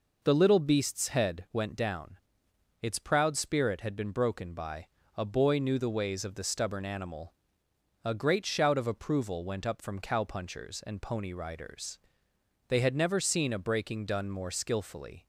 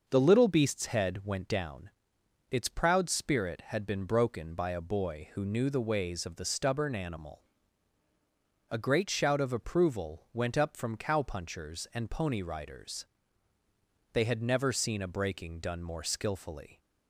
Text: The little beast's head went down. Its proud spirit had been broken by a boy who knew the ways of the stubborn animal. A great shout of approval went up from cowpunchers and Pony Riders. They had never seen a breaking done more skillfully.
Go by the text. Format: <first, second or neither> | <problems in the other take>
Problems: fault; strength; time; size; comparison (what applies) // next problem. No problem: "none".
second | pauses between "by" and "a"; slight; at 4.8 s; 0.30 s long // skips "who"; at 5.5 s